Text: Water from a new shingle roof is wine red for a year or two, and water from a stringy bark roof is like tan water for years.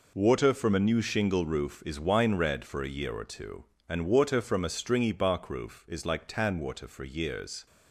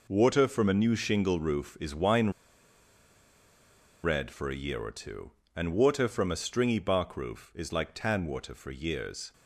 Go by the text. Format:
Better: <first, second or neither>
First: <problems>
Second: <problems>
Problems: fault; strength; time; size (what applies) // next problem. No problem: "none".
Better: first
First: none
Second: pauses between "wine" and "red"; strong; at 2.2 s; 1.7 s long